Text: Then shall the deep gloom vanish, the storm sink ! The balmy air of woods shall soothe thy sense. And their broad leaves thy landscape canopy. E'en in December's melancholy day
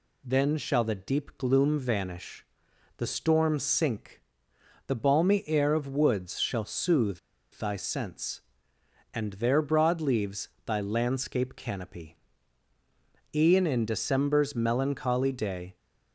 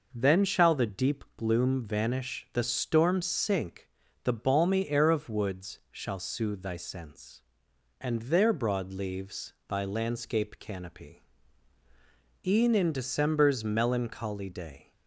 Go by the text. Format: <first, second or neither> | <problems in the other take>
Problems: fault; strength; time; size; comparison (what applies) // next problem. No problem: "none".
second | pauses between "soothe" and "thy"; slight; at 7.1 s; 0.33 s long // pauses between "leaves" and "thy"; slight; at 10.4 s; 0.18 s long